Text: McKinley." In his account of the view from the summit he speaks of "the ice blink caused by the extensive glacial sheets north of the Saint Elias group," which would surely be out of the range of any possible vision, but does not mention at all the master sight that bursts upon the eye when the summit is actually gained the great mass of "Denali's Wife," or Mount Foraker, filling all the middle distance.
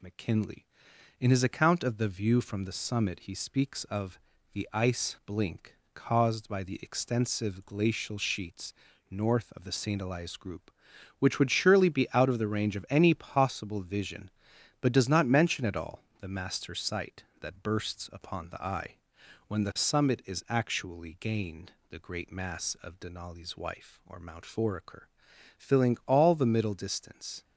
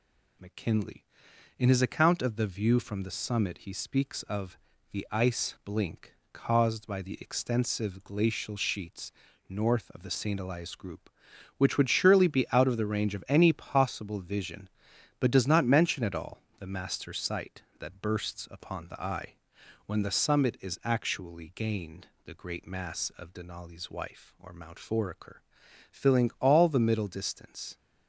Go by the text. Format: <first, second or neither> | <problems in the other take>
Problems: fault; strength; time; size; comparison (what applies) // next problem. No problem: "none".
neither | pauses between "of" and "the"; slight; the same in both // pauses between "blink" and "caused"; slight; the same in both // pauses between "sheets" and "north"; slight; the same in both // pauses between "all" and "the"; slight; the same in both // pauses between "eye" and "when"; noticeable; the same in both // pauses between "gained" and "the"; slight; the same in both